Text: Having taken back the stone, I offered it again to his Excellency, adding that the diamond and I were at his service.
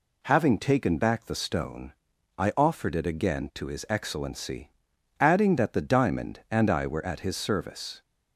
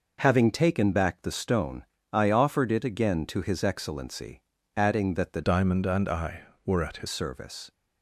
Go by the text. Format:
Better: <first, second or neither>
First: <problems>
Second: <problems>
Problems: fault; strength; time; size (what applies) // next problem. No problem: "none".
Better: first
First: none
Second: changes voice from "diamond" to "his"; from 5.4 to 7.0 s; 1.6 s long